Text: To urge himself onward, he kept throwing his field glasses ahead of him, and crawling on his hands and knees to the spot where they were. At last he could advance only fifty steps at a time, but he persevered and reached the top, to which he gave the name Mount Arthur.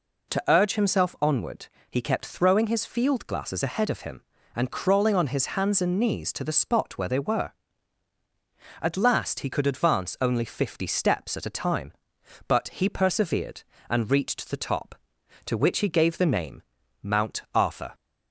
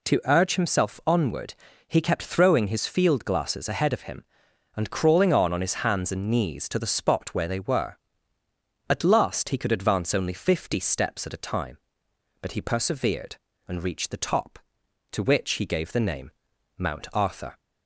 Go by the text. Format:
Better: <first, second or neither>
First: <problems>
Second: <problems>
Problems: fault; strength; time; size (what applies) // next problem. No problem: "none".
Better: first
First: pauses between "name" and "Mount"; at 16.6 s; 0.40 s long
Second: says "on" twice; at 5.5 s // pauses between "name" and "Mount"; noticeable; at 16.3 s; 0.46 s long